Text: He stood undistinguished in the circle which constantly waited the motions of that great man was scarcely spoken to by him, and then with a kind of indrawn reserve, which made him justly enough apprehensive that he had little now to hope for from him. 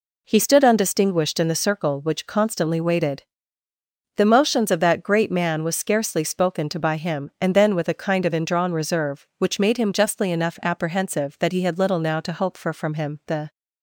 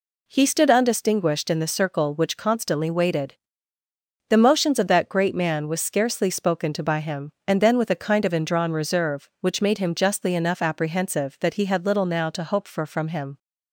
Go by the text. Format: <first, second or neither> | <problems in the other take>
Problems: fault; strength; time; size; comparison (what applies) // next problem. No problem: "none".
second | pauses between "waited" and "the"; noticeable; at 3.2 s; 0.94 s long; noticeable in the second // goes on to say "The"; slight; from 13.2 s on; 0.24 s long